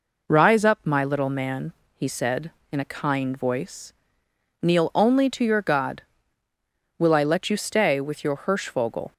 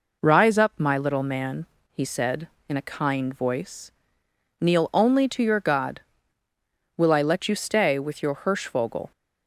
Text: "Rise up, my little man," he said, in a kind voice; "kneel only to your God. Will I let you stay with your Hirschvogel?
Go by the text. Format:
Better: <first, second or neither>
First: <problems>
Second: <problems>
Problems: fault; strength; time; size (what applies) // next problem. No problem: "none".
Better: neither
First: none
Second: none